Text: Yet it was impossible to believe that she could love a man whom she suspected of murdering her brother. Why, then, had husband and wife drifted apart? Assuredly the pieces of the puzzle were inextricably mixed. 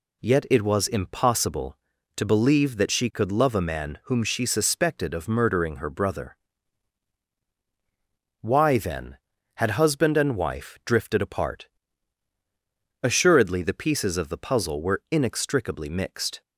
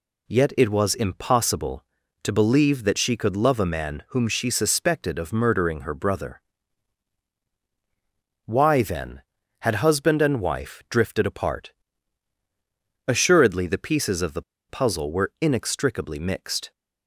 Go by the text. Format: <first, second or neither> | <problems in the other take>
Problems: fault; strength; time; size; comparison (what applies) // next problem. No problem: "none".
first | pauses between "the" and "puzzle"; slight; at 14.4 s; 0.27 s long